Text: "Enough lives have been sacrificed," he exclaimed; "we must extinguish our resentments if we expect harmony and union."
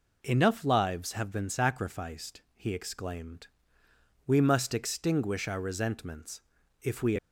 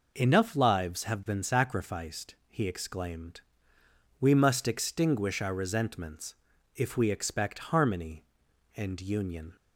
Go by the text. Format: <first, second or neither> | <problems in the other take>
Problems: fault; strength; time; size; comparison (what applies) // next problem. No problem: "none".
second | pauses between "resentments" and "if"; at 6.4 s; 0.40 s long; also in the second // stops before "expect harmony and union"; at 7.1 s